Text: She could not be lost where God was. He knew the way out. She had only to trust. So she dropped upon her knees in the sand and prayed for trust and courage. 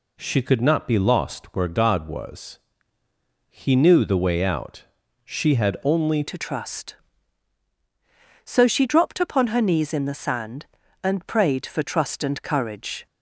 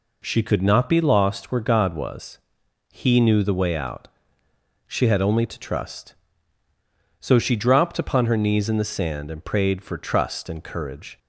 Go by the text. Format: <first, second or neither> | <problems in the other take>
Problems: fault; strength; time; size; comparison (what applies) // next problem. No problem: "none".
second | changes voice at "to"; from 6.2 s on; 6.8 s long